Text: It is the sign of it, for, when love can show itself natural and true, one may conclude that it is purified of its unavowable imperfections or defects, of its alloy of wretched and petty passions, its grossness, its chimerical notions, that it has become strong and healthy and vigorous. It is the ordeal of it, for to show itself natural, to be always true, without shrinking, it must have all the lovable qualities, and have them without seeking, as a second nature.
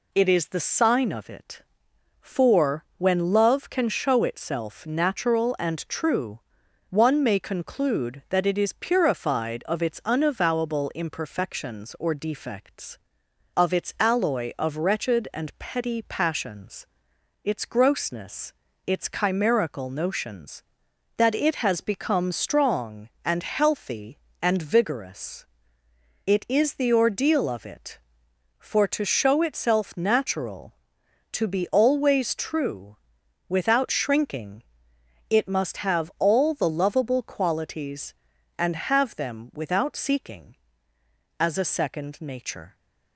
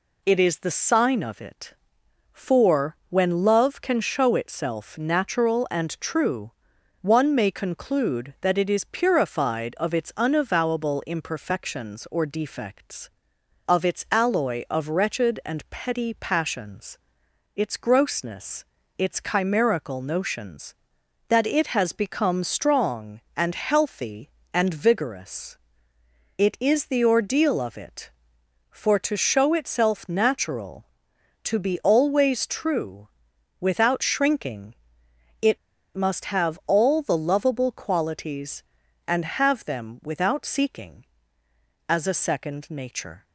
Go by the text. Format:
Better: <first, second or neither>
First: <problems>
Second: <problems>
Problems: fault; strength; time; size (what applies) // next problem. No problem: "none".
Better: first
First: none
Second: pauses between "it" and "must"; at 35.5 s; 0.37 s long